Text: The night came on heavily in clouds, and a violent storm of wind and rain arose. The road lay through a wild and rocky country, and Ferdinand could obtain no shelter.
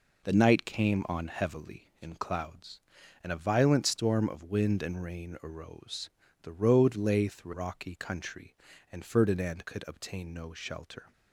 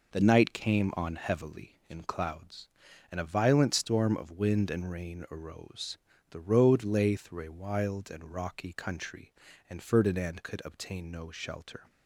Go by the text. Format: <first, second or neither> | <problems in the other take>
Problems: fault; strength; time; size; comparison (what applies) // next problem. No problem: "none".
second | skips "a wild and"; at 7.5 s